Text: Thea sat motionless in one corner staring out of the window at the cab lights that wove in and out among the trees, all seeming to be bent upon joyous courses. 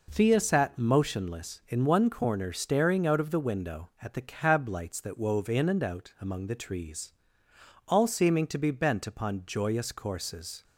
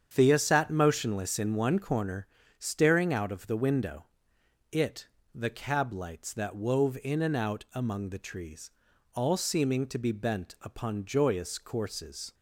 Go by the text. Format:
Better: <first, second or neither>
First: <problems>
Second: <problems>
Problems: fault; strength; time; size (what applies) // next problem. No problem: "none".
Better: first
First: none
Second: starts louder than the rest; strong; until 1.1 s; 8 dB // pauses between "corner" and "staring"; slight; at 2.2 s; 0.32 s long // says "it" for "at"; at 4.6 s